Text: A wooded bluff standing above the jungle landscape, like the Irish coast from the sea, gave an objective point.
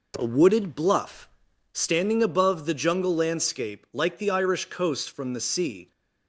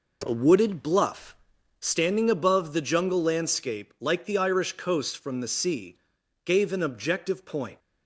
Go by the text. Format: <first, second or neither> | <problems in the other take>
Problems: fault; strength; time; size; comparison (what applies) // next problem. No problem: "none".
second | pauses between "bluff" and "standing"; noticeable; at 1.2 s; 0.46 s long; noticeable in the second // stops before "gave an objective point"; at 5.9 s